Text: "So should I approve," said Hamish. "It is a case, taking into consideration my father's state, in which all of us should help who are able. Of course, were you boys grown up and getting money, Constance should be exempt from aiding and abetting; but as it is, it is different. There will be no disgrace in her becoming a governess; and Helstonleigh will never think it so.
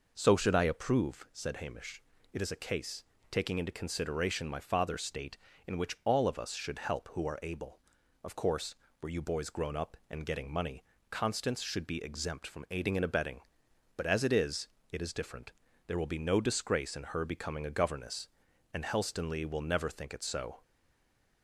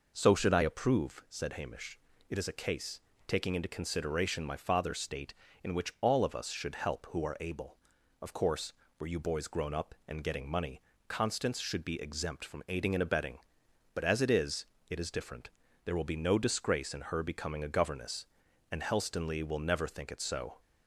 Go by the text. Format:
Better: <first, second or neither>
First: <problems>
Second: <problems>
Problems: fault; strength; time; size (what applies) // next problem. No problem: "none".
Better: second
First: stays silent after the last word; slight; from 20.6 s on; 0.8 s long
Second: none